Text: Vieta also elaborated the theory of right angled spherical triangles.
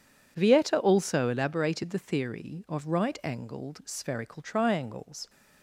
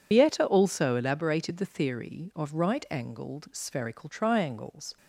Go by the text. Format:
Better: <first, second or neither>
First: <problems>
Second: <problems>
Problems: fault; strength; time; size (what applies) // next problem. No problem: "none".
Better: first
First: none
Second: loses the start of "Vieta"; at 0.1 s; 75 ms